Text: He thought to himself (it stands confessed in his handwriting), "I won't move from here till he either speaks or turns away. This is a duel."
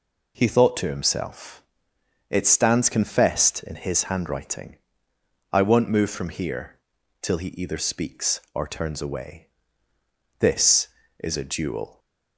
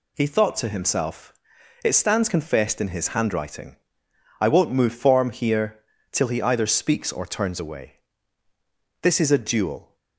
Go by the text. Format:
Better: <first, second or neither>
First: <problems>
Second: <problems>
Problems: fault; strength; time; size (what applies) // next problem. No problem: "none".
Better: first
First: pauses between "here" and "till"; at 6.8 s; 0.42 s long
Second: says "form" for "from"; at 4.9 s // pauses between "here" and "till"; slight; at 5.7 s; 0.32 s long